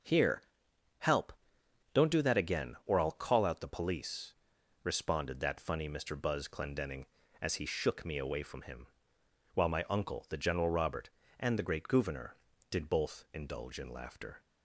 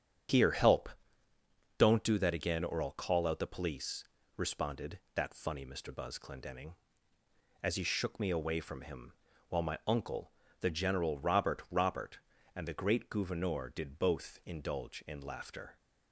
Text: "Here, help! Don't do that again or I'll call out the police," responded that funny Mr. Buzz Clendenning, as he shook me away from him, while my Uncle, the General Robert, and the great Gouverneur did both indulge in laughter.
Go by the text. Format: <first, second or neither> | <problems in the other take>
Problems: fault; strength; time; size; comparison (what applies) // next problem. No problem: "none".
first | starts louder than the rest; strong; until 2.2 s; 8.5 dB // says "Robert" twice; at 11.6 s